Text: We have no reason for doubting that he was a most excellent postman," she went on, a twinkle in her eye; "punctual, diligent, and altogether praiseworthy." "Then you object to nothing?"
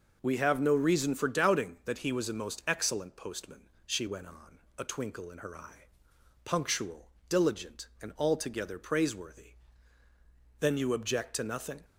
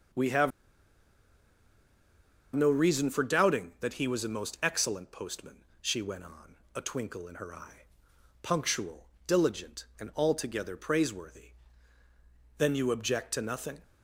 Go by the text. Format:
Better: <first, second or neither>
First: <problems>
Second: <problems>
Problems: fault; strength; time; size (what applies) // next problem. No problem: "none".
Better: first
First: none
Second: pauses between "have" and "no"; strong; at 0.5 s; 2.0 s long